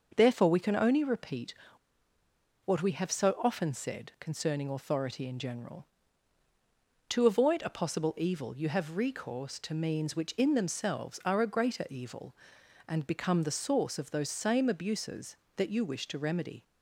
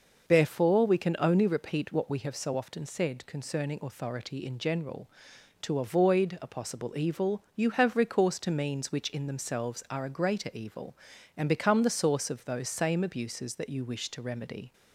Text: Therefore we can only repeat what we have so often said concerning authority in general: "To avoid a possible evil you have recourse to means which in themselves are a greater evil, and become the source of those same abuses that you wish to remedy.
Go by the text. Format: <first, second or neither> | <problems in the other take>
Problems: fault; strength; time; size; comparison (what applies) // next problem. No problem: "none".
second | pauses between "repeat" and "what"; at 1.5 s; 1.1 s long